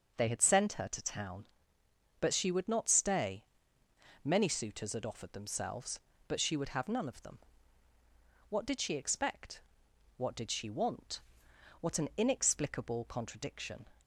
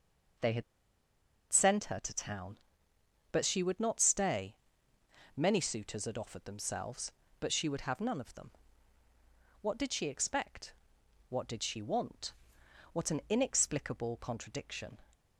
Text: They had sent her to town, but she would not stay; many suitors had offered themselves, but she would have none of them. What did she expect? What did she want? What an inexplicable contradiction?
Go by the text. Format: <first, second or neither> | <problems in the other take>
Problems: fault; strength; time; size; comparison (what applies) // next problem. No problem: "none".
first | pauses between "had" and "sent"; noticeable; at 0.6 s; 0.89 s long